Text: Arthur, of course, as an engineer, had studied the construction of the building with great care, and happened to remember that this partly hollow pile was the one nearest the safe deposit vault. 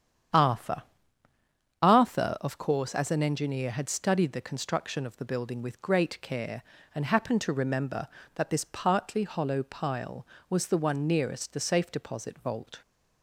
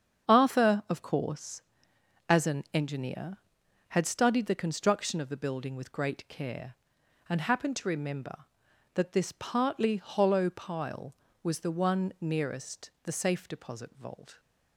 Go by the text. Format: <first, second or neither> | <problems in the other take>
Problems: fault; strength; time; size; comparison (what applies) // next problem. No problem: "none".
second | starts louder than the rest; strong; until 2.3 s; 9 dB; strong in the second // says "Arthur" twice; at 1.8 s